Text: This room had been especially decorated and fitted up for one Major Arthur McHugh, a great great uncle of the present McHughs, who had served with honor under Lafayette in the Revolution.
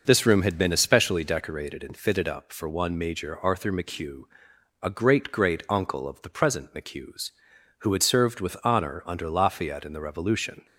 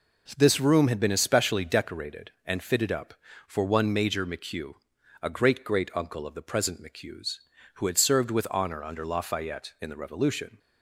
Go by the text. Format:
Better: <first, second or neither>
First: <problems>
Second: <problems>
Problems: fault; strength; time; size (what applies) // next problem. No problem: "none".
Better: first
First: none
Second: skips "Arthur"; at 4.2 s